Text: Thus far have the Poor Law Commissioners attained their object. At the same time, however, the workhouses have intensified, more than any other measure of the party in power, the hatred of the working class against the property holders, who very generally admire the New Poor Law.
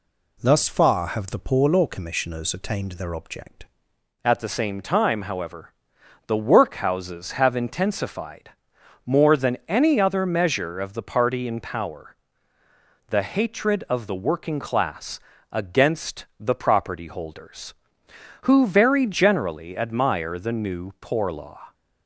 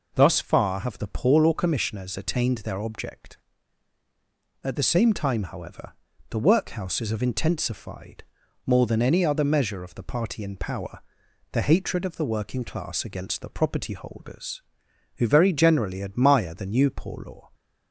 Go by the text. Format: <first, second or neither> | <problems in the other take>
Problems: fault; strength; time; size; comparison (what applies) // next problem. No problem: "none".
second | changes voice at "At"; from 4.2 s on; 17.5 s long // pauses between "class" and "against"; slight; at 15.1 s; 0.32 s long